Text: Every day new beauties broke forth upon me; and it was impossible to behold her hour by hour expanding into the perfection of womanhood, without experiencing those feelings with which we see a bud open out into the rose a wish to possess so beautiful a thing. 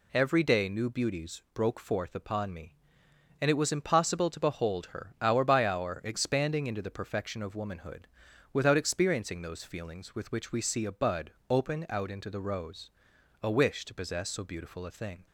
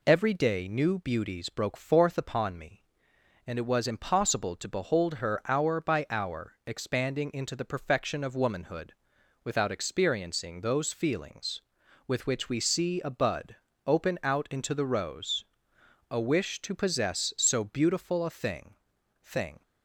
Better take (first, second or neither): first